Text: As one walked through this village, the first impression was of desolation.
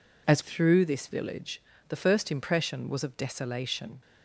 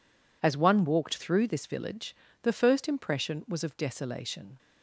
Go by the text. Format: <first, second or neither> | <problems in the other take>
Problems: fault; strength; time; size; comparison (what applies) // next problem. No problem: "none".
second | skips "one walked"; at 0.4 s